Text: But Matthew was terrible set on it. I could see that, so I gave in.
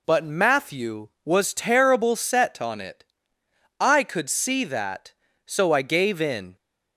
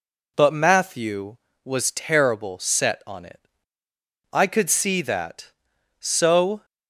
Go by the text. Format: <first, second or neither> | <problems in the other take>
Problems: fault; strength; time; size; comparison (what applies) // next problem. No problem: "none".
first | stops before "I gave in"; at 6.6 s